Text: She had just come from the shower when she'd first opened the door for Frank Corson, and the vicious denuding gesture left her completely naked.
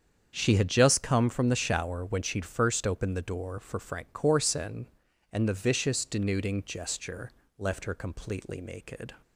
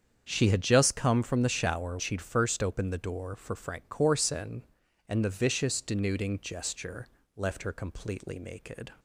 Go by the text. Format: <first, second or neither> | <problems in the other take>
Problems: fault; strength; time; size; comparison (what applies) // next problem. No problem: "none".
first | starts louder than the rest; strong; until 1.3 s; 7.5 dB; strong in the first // skips "when"; at 1.9 s // pauses between "gesture" and "left"; slight; at 7.0 s; 0.30 s long; slight in the first